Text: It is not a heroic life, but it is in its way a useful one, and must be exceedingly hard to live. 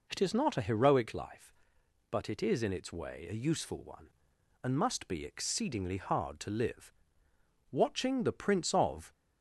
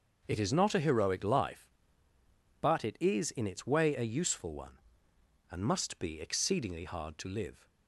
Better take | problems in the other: second | goes on to say "Watching the Prince of"; from 7.7 s on; 1.4 s long

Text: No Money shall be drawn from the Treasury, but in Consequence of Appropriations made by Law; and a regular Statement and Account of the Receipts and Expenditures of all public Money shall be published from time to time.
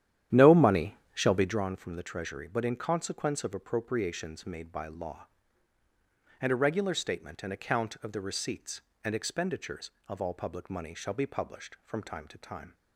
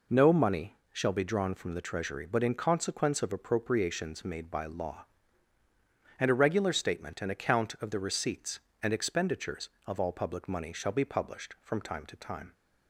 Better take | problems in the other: second | starts louder than the rest; strong; until 1.6 s; 11 dB // pauses between "Money" and "shall"; slight; at 0.9 s; 0.16 s long; slight in the second

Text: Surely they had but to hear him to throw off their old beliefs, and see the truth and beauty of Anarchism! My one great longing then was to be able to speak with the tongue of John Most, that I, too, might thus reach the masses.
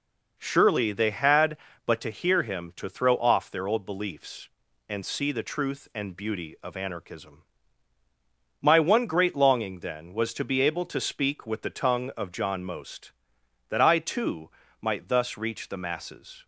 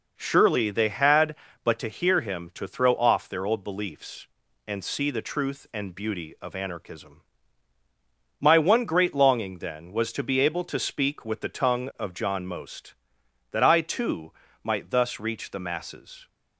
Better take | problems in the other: neither | none

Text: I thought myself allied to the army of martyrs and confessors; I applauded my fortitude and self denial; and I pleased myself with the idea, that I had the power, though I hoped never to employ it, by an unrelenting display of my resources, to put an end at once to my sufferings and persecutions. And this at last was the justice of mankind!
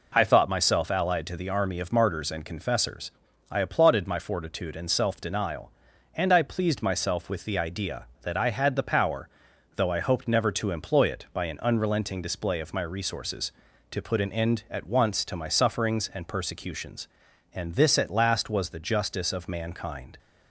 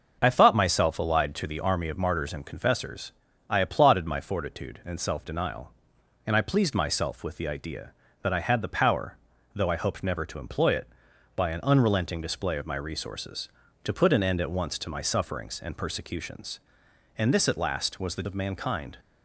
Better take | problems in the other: first | starts louder than the rest; until 1.2 s; 6.5 dB // skips "justice"; at 18.2 s

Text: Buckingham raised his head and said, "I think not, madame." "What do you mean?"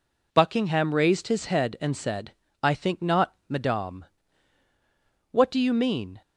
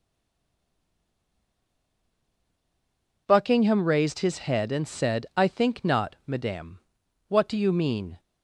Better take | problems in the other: first | stays silent before the first word; strong; until 3.2 s; 3.2 s long

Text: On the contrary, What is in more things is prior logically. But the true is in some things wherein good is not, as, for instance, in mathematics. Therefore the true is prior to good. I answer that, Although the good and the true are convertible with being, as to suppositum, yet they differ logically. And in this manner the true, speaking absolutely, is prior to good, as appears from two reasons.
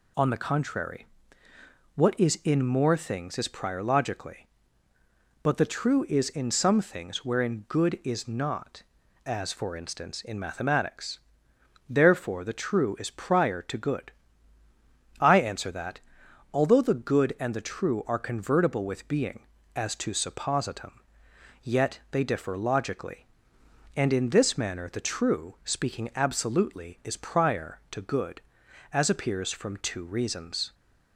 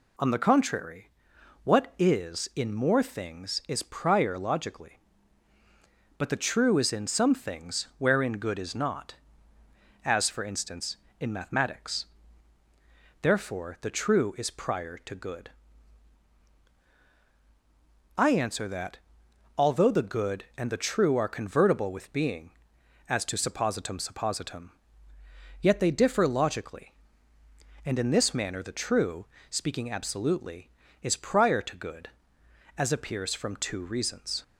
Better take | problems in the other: first | says "suppositum" twice; at 23.9 s

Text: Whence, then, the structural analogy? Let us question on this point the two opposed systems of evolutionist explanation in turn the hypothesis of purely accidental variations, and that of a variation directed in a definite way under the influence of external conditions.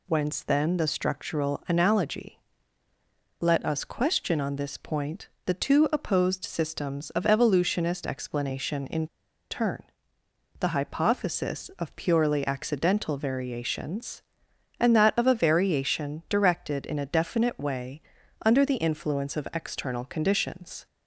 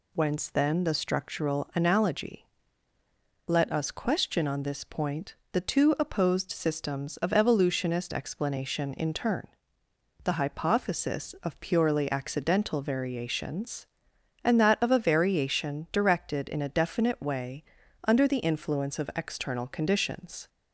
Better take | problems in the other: second | pauses between "point" and "the"; slight; at 5.2 s; 0.18 s long; slight in the second // pauses between "in" and "turn"; at 9.0 s; 0.45 s long // pauses between "turn" and "the"; noticeable; at 9.8 s; 0.78 s long; noticeable in the second // pauses between "way" and "under"; at 18.0 s; 0.42 s long; also in the second

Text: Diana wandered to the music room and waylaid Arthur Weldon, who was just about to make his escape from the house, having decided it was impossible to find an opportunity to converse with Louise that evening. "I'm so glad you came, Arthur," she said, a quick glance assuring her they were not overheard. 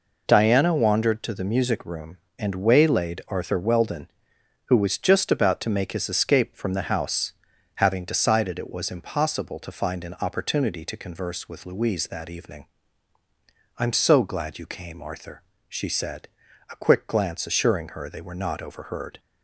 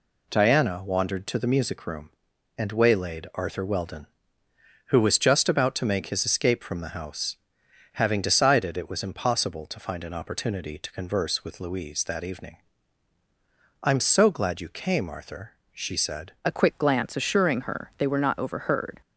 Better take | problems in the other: first | changes voice at "a"; from 16.4 s on; 2.5 s long

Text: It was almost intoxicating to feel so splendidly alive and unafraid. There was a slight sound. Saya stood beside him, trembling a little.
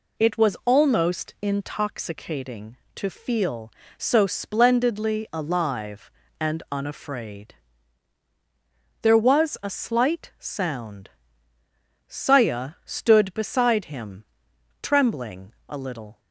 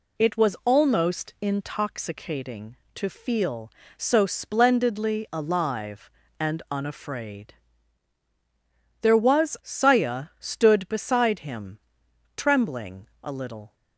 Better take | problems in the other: first | skips "a slight sound"; at 9.5 s // pauses between "trembling" and "a"; slight; at 13.0 s; 0.16 s long; slight in the first

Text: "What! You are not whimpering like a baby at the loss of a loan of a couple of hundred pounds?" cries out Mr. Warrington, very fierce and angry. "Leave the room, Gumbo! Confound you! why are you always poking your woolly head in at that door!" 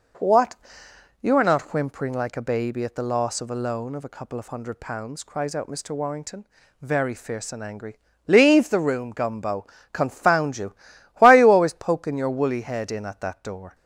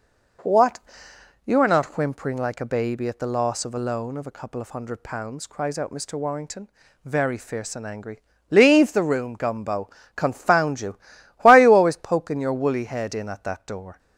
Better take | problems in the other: neither | none

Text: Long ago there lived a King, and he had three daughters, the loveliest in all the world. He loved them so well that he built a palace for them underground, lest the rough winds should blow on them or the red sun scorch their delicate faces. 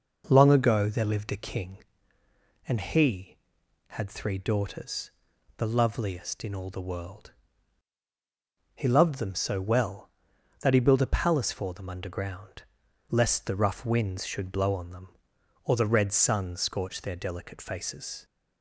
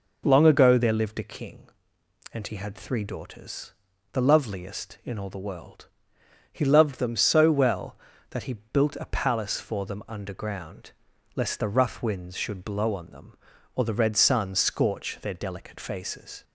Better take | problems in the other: neither | none

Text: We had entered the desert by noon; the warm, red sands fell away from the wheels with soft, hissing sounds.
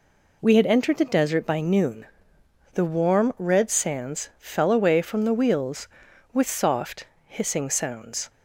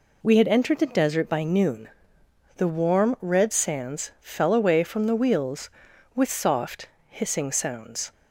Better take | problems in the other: neither | none

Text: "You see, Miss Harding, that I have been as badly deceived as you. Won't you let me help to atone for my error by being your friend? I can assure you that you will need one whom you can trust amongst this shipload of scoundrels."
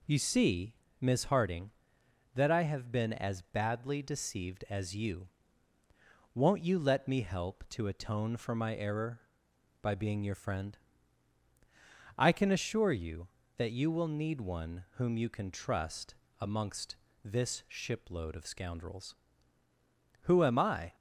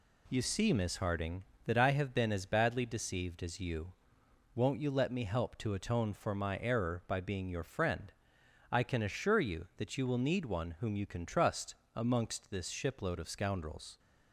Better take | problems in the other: second | pauses between "trust" and "amongst"; slight; at 16.1 s; 0.26 s long; slight in the second // pauses between "amongst" and "this"; slight; at 16.9 s; 0.28 s long // goes on to say "Who am I"; noticeable; from 20.2 s on; 0.72 s long

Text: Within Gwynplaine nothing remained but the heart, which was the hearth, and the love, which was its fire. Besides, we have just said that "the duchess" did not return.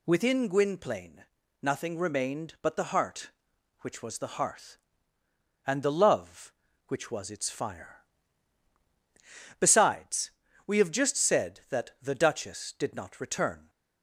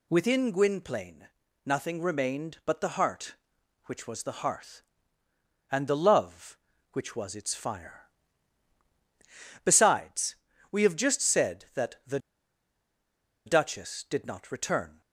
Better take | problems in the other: first | pauses between "Gwynplaine" and "nothing"; at 1.2 s; 0.40 s long; also in the first // pauses between "the" and "duchess"; strong; at 12.1 s; 1.2 s long

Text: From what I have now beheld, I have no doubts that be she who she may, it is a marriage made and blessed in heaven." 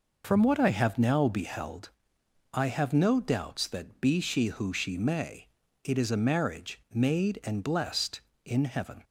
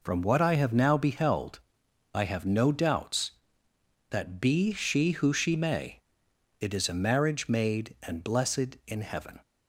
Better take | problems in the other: neither | none

